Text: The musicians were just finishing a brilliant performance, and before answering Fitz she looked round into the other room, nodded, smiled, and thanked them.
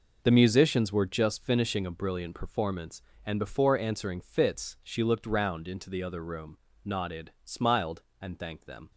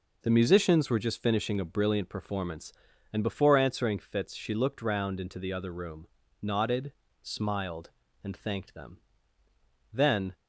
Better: first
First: none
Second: goes on to say "Then"; slight; from 9.9 s on; 0.42 s long

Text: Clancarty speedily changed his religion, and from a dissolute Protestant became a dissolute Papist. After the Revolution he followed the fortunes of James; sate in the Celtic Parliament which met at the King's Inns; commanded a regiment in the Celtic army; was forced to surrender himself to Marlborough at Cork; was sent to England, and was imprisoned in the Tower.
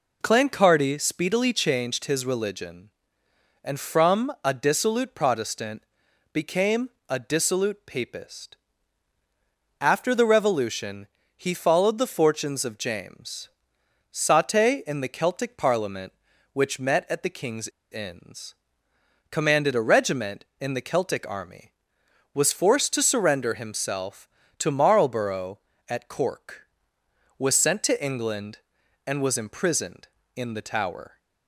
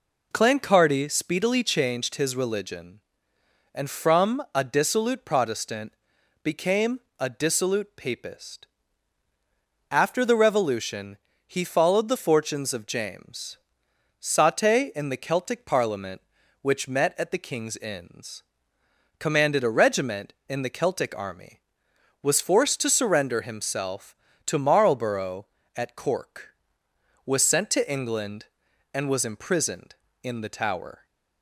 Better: second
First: pauses between "Protestant" and "became"; noticeable; at 5.8 s; 0.50 s long // pauses between "became" and "a"; slight; at 6.8 s; 0.20 s long // pauses between "Revolution" and "he"; slight; at 11.0 s; 0.28 s long // pauses between "King's" and "Inns"; slight; at 17.6 s; 0.23 s long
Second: pauses between "Protestant" and "became"; noticeable; at 5.9 s; 0.50 s long // pauses between "became" and "a"; slight; at 6.9 s; 0.20 s long // pauses between "Revolution" and "he"; slight; at 11.1 s; 0.28 s long

